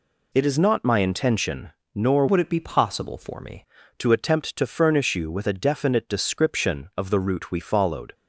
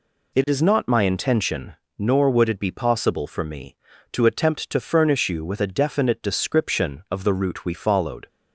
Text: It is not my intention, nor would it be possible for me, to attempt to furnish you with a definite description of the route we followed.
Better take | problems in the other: second | changes voice from "would" to "me"; from 2.2 to 3.6 s; 1.4 s long

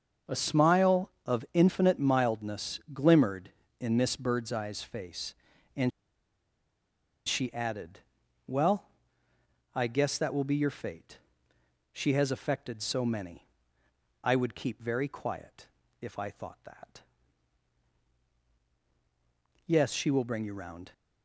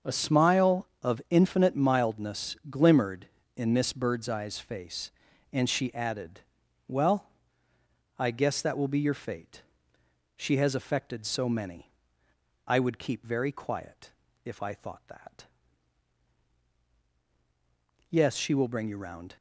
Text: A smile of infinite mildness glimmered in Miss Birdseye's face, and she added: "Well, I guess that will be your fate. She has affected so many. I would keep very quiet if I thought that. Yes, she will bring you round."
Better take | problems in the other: second | starts louder than the rest; until 1.4 s; 6.5 dB; also in the second // pauses between "and" and "she"; strong; at 5.9 s; 1.3 s long // pauses between "quiet" and "if"; slight; at 15.6 s; 0.34 s long; slight in the second

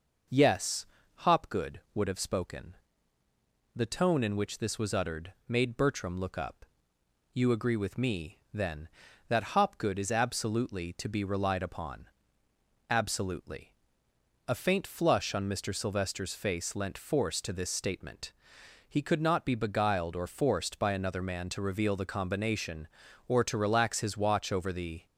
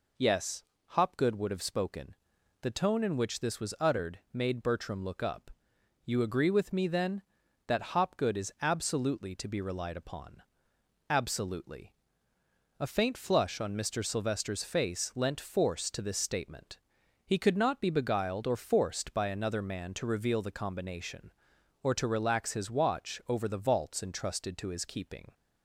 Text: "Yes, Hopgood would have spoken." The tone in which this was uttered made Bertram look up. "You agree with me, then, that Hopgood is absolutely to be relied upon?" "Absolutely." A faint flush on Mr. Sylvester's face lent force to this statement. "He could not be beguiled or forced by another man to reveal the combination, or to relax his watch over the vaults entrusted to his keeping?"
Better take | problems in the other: second | pauses between "uttered" and "made"; slight; at 5.3 s; 0.16 s long // stops before "vaults entrusted to his keeping"; at 25.0 s

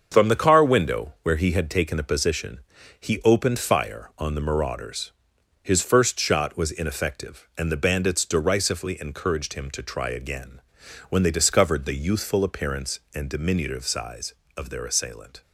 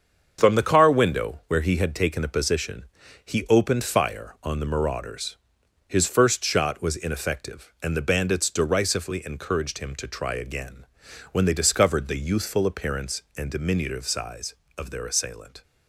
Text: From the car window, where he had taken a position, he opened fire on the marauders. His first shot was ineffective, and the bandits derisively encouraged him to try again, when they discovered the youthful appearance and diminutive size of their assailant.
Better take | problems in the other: neither | starts louder than the rest; the same in both

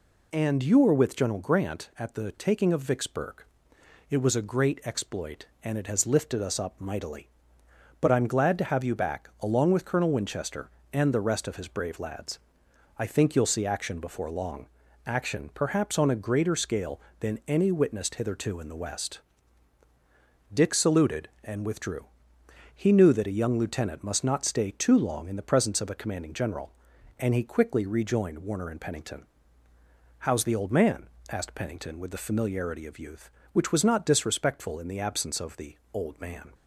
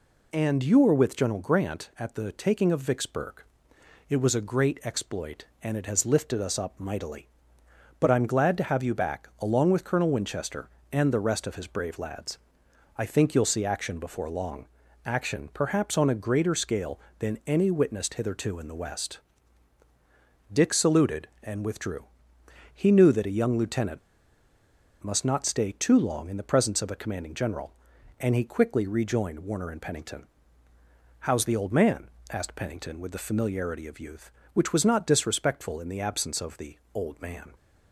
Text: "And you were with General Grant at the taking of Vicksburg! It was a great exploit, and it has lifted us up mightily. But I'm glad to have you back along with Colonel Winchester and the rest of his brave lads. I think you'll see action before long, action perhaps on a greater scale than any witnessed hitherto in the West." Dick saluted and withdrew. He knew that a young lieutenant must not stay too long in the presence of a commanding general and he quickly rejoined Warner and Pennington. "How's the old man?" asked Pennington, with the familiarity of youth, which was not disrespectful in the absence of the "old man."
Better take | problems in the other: first | pauses between "lieutenant" and "must"; at 23.9 s; 1.0 s long // pauses between "the" and "old"; slight; at 36.7 s; 0.18 s long; slight in the first

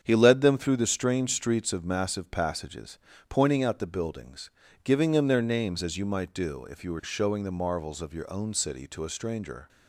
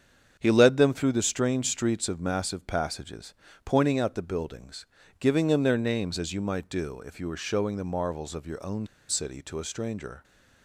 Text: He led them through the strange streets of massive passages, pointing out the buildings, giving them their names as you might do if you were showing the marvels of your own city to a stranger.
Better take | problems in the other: first | starts louder than the rest; strong; until 1.4 s; 7.5 dB; strong in the first // pauses between "own" and "city"; slight; at 8.8 s; 0.23 s long

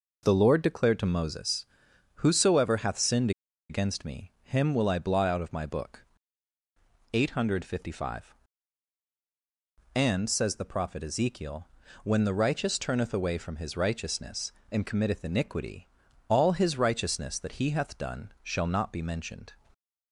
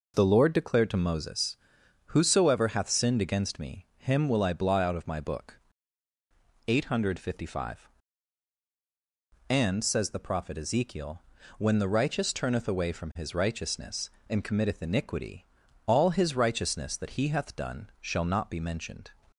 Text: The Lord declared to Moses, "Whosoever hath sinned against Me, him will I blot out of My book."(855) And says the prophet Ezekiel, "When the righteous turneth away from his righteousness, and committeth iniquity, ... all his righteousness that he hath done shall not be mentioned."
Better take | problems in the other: second | pauses between "sinned" and "against"; at 3.2 s; 0.39 s long

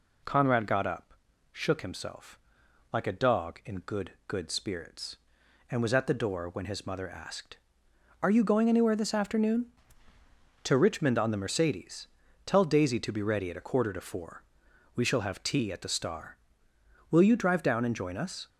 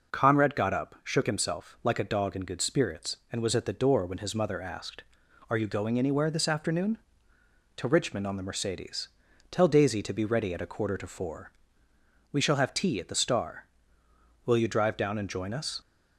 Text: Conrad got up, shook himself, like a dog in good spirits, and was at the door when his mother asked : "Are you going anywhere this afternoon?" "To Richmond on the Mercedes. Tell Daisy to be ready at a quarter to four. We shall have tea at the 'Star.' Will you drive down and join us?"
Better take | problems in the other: second | says "good" twice; at 4.2 s

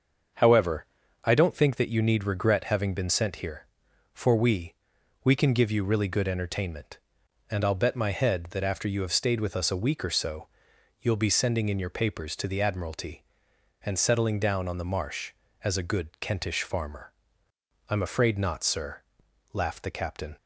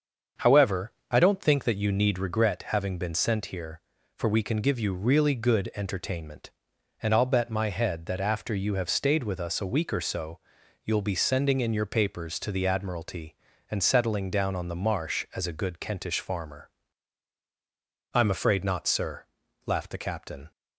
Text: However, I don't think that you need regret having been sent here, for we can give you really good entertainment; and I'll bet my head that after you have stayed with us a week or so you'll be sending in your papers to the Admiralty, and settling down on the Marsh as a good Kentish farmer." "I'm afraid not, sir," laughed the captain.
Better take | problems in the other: second | starts louder than the rest; until 1.7 s; 6.5 dB; also in the second // says "we" twice; at 5.2 s // pauses between "so" and "you'll"; noticeable; at 10.4 s; 0.52 s long; noticeable in the second

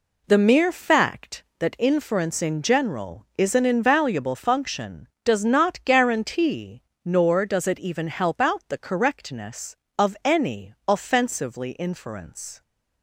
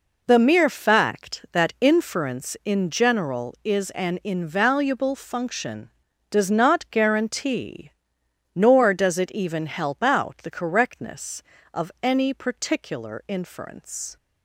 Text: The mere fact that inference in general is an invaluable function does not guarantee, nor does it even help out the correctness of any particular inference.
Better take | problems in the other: second | says "offensively" for "particular"; at 10.8 s

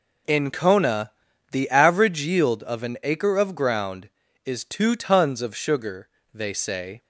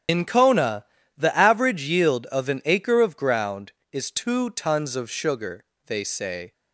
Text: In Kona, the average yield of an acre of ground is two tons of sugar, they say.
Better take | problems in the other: first | loses the start of "In"; at 0.0 s; 50 ms // starts louder than the rest; strong; until 1.4 s; 9 dB

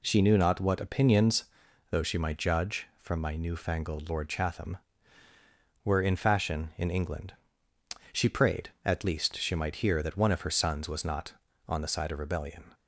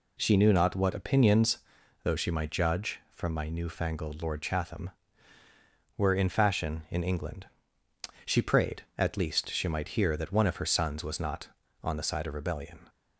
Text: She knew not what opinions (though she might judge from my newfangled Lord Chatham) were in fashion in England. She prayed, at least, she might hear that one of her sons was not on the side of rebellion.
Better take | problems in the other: neither | none

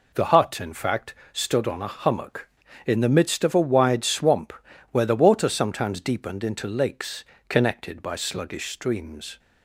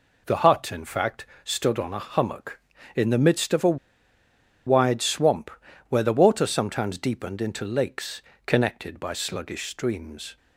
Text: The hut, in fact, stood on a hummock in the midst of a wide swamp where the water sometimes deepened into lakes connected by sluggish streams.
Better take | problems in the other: first | pauses between "a" and "wide"; noticeable; at 3.7 s; 0.90 s long // pauses between "swamp" and "where"; at 5.5 s; 0.40 s long; also in the first // pauses between "lakes" and "connected"; slight; at 8.2 s; 0.24 s long; slight in the first

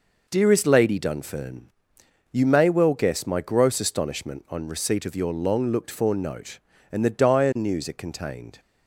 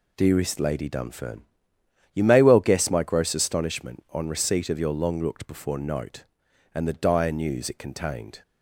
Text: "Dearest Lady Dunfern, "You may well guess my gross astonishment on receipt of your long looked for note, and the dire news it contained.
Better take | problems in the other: first | says "before" for "for"; at 5.4 s

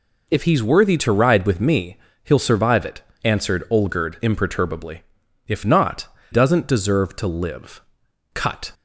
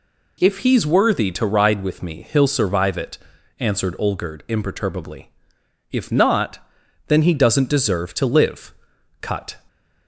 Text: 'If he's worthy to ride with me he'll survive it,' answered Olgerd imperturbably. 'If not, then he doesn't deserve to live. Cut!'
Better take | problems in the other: second | pauses between "me" and "he'll"; slight; at 1.9 s; 0.26 s long // skips "then he"; at 6.1 s

